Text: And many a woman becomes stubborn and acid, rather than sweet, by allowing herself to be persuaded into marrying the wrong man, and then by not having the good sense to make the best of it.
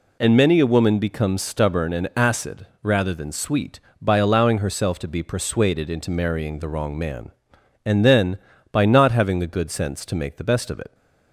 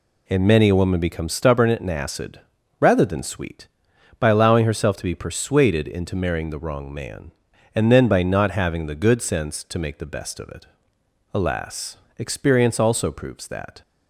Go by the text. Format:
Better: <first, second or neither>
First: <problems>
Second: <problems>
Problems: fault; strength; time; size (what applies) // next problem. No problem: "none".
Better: first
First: none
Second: goes on to say "Alas experience also proves that"; strong; from 11.3 s on; 2.4 s long